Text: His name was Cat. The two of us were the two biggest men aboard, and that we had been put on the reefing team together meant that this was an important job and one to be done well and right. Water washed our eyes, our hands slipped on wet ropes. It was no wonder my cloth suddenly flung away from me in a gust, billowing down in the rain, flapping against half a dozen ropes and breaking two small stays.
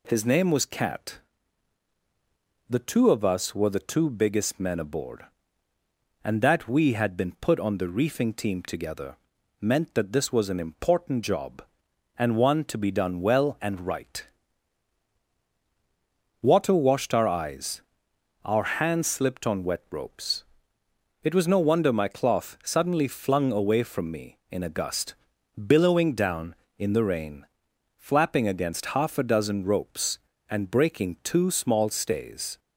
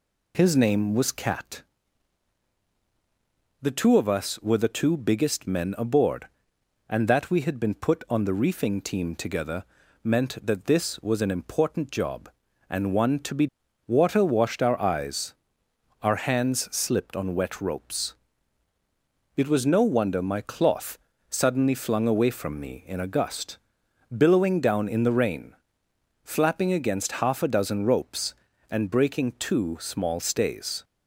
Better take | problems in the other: first | pauses between "together" and "meant"; at 9.6 s; 0.40 s long; also in the first // skips "done well and right"; at 13.6 s // pauses between "cloth" and "suddenly"; slight; at 20.9 s; 0.28 s long

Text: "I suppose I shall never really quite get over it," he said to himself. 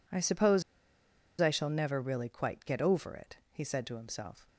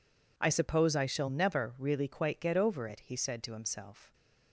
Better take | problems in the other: second | pauses between "suppose" and "I"; noticeable; at 0.6 s; 0.78 s long

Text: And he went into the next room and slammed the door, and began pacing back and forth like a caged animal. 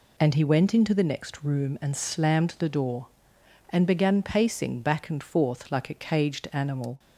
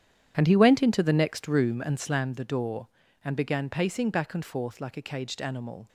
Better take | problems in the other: first | starts louder than the rest; strong; until 2.0 s; 9.5 dB

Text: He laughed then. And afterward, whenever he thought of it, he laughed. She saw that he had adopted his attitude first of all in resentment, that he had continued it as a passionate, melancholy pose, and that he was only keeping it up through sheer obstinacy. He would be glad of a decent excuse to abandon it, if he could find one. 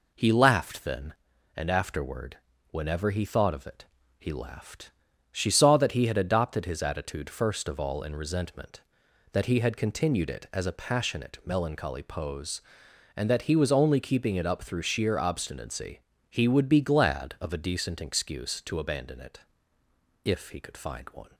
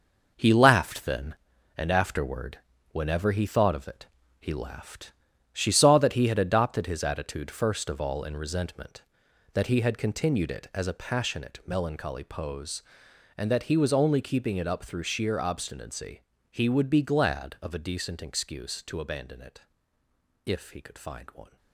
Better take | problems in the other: first | gets quieter; strong; throughout; 8.5 dB

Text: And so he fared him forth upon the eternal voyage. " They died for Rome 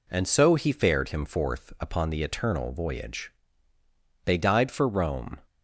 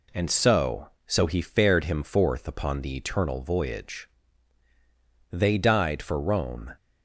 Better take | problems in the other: first | says "so" twice; at 1.0 s

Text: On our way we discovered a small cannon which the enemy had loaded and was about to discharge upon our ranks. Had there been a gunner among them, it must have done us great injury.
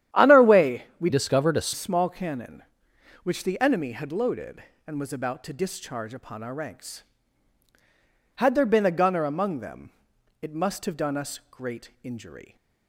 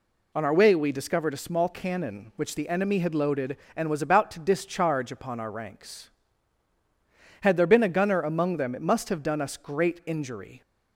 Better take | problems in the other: second | starts louder than the rest; strong; until 1.3 s; 11 dB // pauses between "way" and "we"; slight; at 0.8 s; 0.16 s long // changes voice from "discovered" to "a"; from 1.1 to 1.7 s; 0.6 s long

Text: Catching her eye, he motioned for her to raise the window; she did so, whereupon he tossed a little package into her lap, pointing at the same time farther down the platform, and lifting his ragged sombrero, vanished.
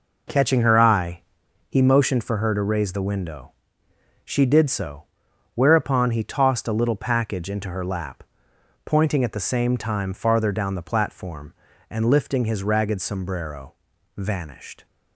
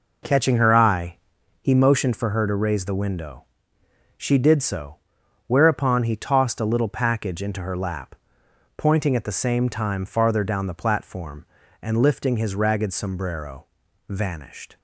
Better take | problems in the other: neither | none

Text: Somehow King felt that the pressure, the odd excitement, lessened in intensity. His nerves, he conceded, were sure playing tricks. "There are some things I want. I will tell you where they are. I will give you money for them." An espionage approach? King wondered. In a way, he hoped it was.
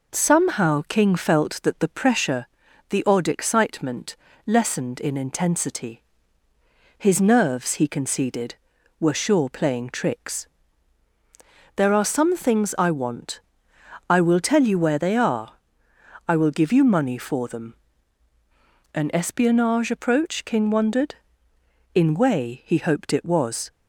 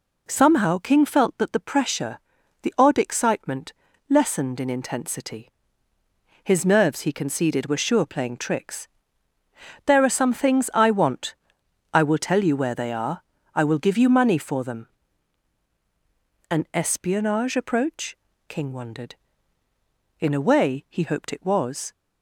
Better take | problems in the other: second | skips "a"; at 22.1 s

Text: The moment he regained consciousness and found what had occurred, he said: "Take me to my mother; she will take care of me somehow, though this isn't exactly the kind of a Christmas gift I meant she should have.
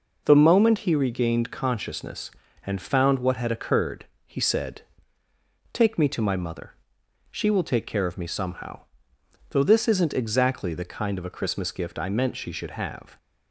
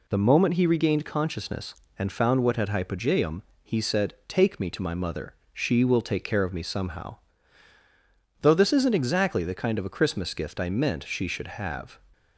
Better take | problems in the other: first | says "hypogeum" for "occurred"; at 2.6 s

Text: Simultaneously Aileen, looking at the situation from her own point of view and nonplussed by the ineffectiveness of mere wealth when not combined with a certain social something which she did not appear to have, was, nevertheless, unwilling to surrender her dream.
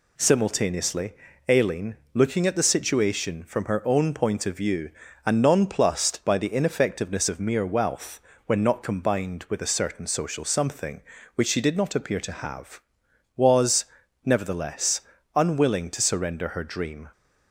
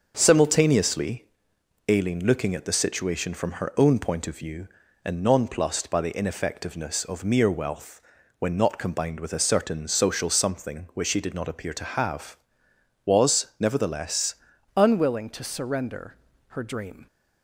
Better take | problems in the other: first | starts louder than the rest; noticeable; until 1.1 s; 6 dB // pauses between "Simultaneously" and "Aileen"; noticeable; at 1.2 s; 0.64 s long; slight in the first // pauses between "wealth" and "when"; at 7.9 s; 0.40 s long; slight in the first // changes voice at "unwilling"; from 14.7 s on; 2.3 s long // pauses between "surrender" and "her"; slight; at 16.1 s; 0.34 s long

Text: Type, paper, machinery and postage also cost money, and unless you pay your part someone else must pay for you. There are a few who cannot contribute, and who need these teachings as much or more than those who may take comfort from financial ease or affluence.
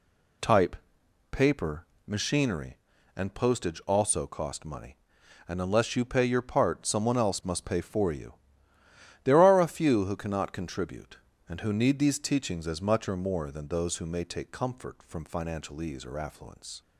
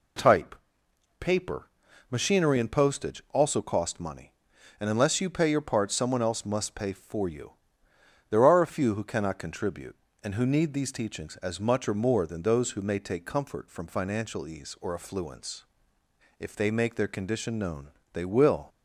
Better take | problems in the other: first | goes on to say "If they make their condition known they will"; strong; from 16.3 s on; 2.2 s long

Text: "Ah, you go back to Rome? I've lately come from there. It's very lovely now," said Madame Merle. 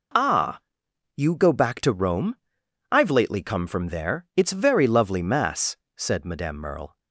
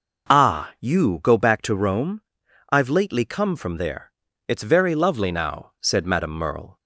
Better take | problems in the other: second | says "mass" for "now"; at 5.2 s

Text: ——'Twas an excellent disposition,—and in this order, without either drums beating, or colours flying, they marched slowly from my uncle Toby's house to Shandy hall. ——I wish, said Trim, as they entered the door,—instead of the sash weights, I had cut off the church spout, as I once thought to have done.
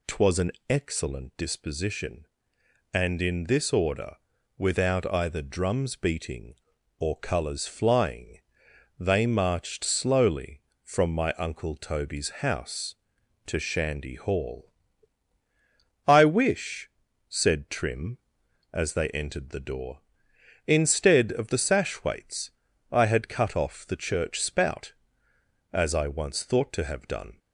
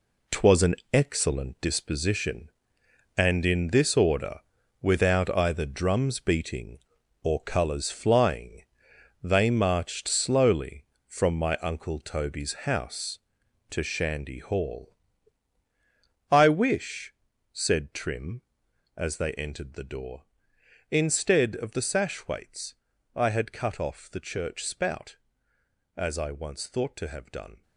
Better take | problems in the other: first | gets quieter; strong; throughout; 9 dB // pauses between "an" and "excellent"; slight; at 0.7 s; 0.16 s long; slight in the first

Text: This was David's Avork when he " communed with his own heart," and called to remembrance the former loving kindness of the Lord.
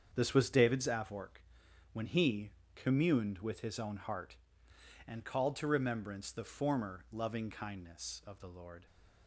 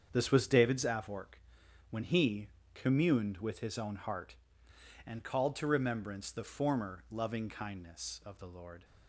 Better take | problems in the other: neither | starts louder than the rest; strong; the same in both // pauses between "Avork" and "when"; noticeable; the same in both

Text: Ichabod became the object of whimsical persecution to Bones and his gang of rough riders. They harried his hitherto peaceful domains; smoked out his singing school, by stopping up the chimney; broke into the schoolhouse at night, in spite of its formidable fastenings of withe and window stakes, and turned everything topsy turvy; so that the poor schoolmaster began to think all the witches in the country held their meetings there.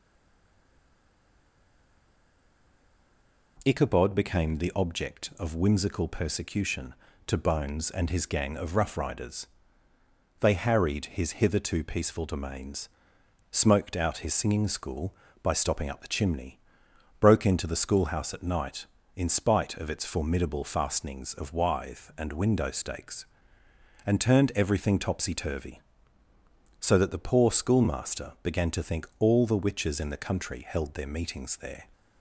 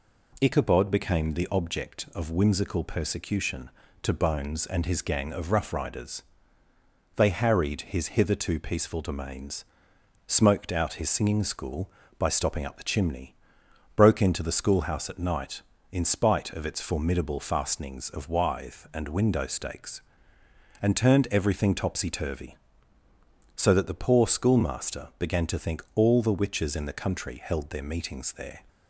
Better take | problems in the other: second | stays silent before the first word; strong; until 3.5 s; 3.5 s long

